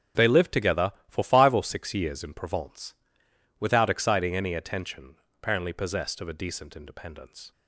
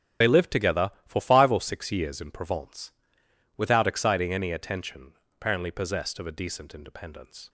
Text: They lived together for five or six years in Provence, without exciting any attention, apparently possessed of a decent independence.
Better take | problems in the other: first | loses the start of "They"; at 0.2 s; 55 ms // starts louder than the rest; strong; until 1.3 s; 9 dB; strong in the first

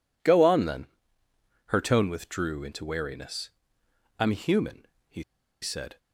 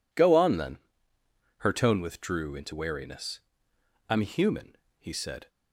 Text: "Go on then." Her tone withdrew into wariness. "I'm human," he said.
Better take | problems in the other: second | pauses between "he" and "said"; at 5.2 s; 0.38 s long

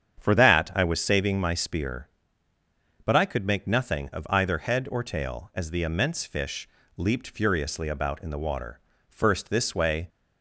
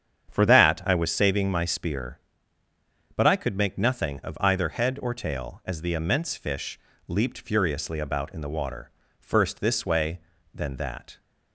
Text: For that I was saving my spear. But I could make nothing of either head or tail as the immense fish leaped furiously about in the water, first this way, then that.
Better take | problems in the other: second | starts louder than the rest; strong; until 1.2 s; 8 dB; strong in the second // pauses between "fish" and "leaped"; slight; at 6.6 s; 0.28 s long; slight in the second // stops before "then that"; at 10.0 s

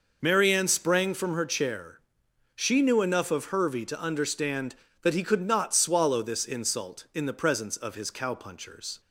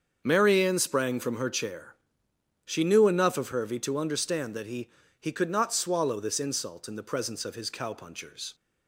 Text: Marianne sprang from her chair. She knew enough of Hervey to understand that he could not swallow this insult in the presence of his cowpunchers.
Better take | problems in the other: first | starts louder than the rest; until 1.2 s; 6.5 dB // says "he" twice; at 5.1 s

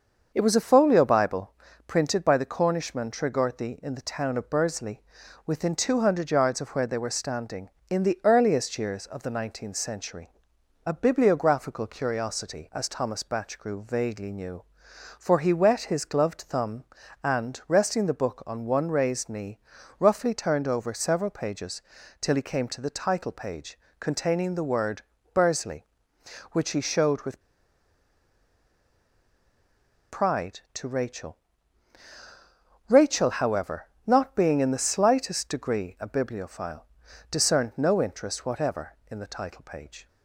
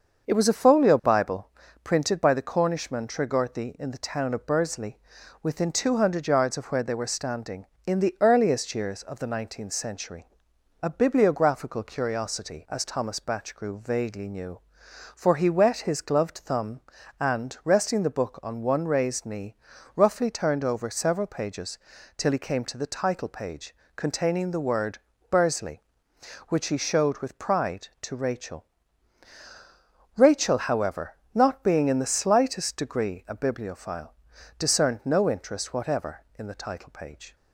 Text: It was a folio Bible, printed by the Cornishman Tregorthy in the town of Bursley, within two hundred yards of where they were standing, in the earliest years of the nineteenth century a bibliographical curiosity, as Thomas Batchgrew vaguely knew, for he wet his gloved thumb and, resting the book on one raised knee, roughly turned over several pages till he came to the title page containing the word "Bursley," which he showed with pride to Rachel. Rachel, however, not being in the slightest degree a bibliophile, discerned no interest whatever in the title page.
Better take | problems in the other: second | starts louder than the rest; until 1.3 s; 6.5 dB; also in the second // pauses between "century" and "a"; noticeable; at 10.2 s; 0.58 s long; noticeable in the second // pauses between "pages" and "till"; at 21.8 s; 0.38 s long; also in the second // pauses between "page" and "containing"; slight; at 23.7 s; 0.22 s long; slight in the second // pauses between "word" and "Bursley"; slight; at 25.0 s; 0.32 s long; slight in the second // pauses between "with" and "pride"; strong; at 27.4 s; 2.6 s long

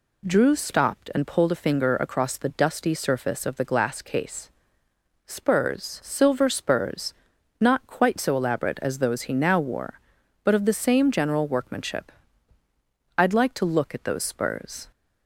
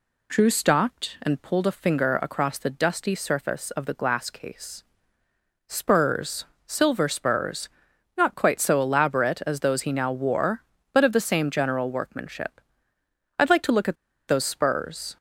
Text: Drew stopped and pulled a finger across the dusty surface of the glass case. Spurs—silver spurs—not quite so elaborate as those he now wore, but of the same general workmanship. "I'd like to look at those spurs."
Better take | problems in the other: first | pauses between "at" and "those"; slight; at 13.9 s; 0.32 s long

